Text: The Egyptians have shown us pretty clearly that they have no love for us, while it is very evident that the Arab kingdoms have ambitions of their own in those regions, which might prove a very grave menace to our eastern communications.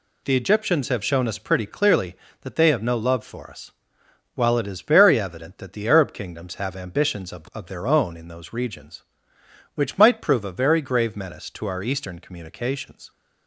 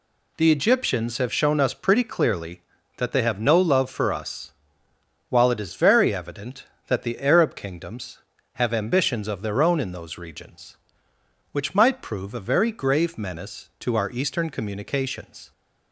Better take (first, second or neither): second